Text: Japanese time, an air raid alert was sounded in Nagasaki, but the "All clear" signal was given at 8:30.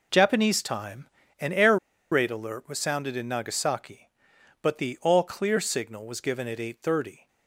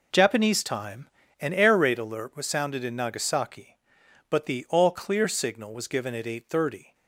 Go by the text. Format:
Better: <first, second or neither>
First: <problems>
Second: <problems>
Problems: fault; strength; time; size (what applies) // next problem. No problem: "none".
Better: second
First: pauses between "air" and "raid"; slight; at 1.7 s; 0.35 s long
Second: none